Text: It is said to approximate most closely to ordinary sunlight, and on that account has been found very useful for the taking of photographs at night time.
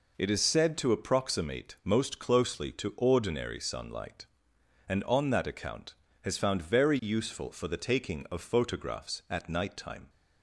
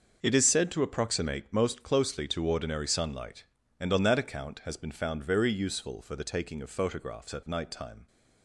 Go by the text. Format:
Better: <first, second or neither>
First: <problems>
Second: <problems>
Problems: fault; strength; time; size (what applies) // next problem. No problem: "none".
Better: second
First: skips "been"; at 6.3 s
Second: none